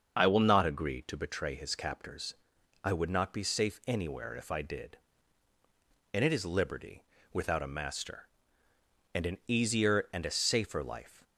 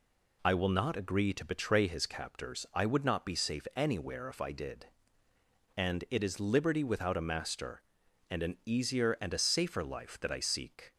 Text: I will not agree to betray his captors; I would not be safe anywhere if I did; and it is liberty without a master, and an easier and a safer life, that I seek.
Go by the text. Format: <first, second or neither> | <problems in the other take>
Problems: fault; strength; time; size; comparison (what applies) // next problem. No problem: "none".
second | starts louder than the rest; until 1.2 s; 6.5 dB // pauses between "liberty" and "without"; slight; at 7.0 s; 0.28 s long // stops before "that I seek"; at 11.2 s